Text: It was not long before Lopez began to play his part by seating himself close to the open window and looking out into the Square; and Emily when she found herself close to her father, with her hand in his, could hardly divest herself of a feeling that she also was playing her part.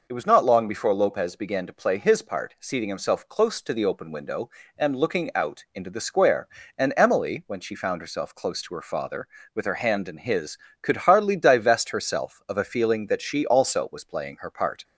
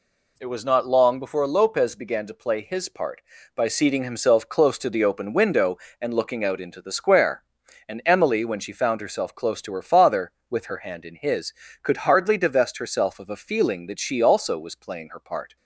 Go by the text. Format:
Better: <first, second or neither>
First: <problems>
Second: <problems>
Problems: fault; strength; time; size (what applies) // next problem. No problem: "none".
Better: second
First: skips "by"; at 2.5 s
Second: none